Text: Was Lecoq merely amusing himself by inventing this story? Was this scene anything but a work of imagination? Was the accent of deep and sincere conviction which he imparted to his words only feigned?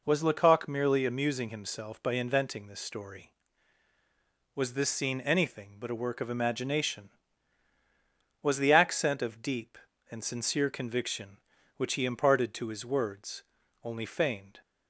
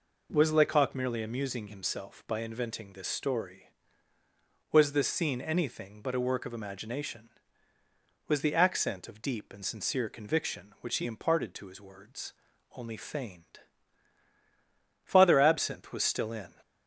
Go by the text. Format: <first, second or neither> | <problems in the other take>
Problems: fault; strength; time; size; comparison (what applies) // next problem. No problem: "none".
first | pauses between "words" and "only"; noticeable; at 12.3 s; 0.46 s long; also in the first // goes on to say "Father Absinthe was still in"; from 15.0 s on; 1.4 s long